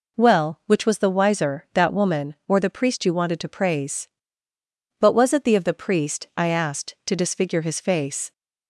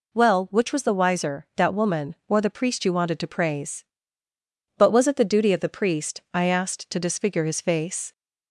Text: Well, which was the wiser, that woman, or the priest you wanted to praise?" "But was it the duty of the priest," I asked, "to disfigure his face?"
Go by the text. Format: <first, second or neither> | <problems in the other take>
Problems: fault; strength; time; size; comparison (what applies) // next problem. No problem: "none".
second | skips "duty"; at 5.5 s